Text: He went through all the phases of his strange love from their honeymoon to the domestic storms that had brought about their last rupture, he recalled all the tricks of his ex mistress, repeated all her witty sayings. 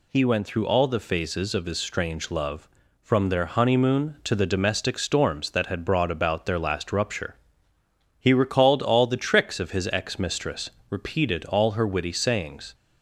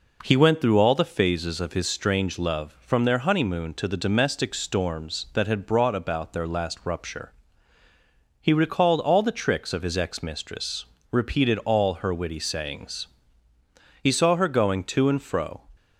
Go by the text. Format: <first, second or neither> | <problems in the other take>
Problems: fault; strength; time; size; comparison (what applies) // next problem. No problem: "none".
first | goes on to say "He saw her going to and fro"; from 14.0 s on; 1.6 s long